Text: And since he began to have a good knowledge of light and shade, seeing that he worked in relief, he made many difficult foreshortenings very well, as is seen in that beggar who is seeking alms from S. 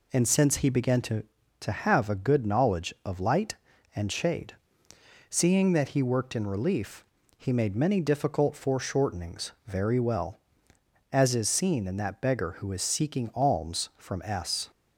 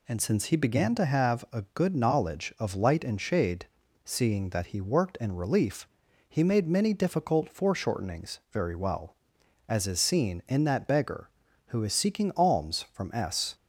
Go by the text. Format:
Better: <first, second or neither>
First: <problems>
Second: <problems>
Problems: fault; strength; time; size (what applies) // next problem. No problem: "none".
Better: second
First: says "to" twice; at 1.6 s // pauses between "foreshortenings" and "very"; slight; at 9.5 s; 0.16 s long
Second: none